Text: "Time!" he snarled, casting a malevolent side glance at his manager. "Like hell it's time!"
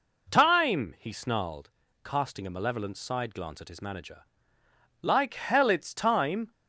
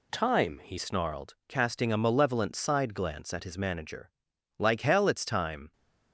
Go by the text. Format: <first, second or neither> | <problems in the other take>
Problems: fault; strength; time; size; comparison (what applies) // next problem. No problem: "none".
first | changes voice at "snarled"; from 0.7 s on; 5.0 s long